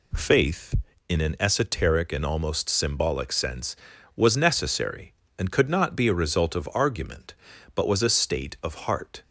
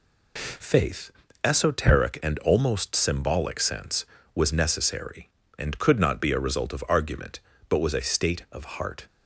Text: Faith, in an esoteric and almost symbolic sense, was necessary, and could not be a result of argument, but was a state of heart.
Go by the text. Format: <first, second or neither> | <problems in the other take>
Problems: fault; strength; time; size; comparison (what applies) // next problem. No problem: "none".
first | skips "in an"; at 1.2 s